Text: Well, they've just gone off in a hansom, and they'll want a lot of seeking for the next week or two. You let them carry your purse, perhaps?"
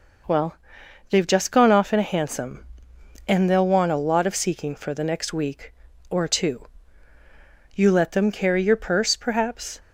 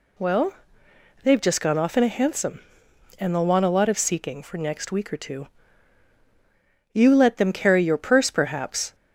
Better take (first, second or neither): first